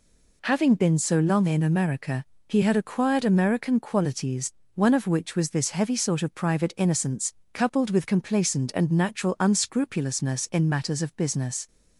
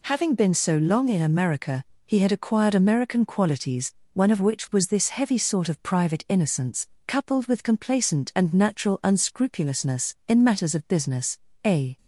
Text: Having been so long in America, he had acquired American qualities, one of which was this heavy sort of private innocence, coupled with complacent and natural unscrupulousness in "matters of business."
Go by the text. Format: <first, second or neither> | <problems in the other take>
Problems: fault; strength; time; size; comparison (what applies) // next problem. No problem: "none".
first | goes on to say "A"; slight; from 11.6 s on; 0.32 s long